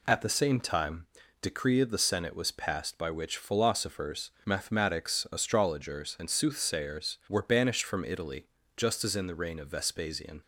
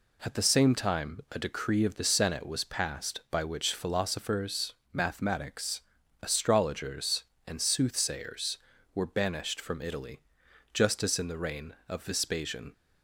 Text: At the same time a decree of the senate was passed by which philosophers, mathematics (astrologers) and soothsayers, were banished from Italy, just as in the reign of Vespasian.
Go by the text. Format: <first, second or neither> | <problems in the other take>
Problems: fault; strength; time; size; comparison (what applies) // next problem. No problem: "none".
second | skips "a"; at 1.2 s